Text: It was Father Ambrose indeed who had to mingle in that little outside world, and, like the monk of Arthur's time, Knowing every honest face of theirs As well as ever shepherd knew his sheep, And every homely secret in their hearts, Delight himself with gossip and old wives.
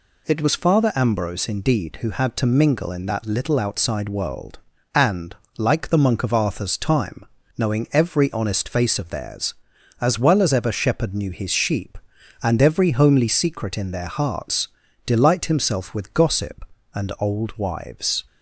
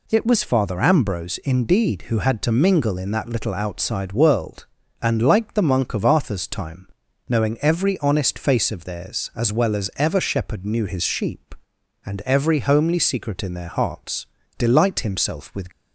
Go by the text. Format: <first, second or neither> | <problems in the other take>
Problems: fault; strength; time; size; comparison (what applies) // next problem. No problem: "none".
first | stops before "gossip and old wives"; at 15.7 s